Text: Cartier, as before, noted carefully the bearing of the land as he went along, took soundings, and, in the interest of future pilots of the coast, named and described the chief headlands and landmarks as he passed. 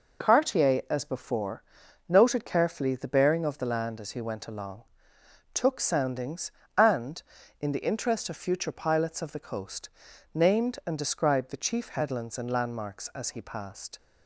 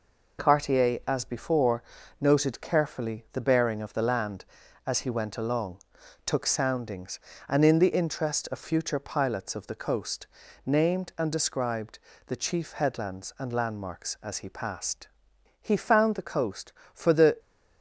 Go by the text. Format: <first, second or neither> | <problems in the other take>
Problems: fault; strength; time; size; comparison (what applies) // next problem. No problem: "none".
first | pauses between "described" and "the"; slight; at 11.9 s; 0.26 s long // goes on to say "He found the coast for the"; strong; from 15.6 s on; 1.7 s long